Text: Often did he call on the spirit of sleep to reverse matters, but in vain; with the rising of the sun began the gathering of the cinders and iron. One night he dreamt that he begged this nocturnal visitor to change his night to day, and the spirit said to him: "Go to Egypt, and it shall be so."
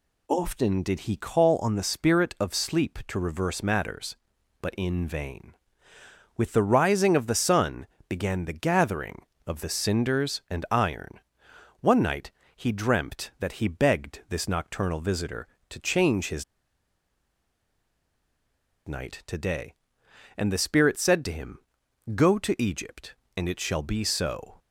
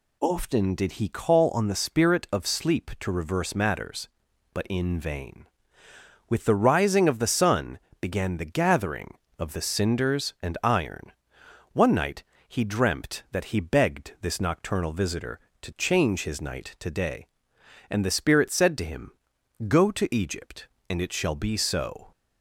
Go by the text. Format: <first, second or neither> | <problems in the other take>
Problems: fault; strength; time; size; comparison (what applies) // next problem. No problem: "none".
second | pauses between "sun" and "began"; slight; at 7.8 s; 0.22 s long; slight in the second // pauses between "night" and "he"; slight; at 12.3 s; 0.26 s long; slight in the second // pauses between "his" and "night"; strong; at 16.4 s; 2.4 s long